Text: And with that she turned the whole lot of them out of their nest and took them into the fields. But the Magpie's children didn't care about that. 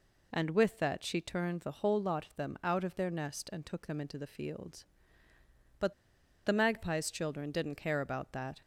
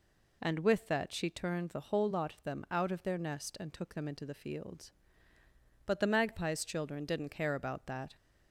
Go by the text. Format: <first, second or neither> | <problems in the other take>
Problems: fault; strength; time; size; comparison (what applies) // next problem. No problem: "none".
second | pauses between "But" and "the"; noticeable; at 5.9 s; 0.53 s long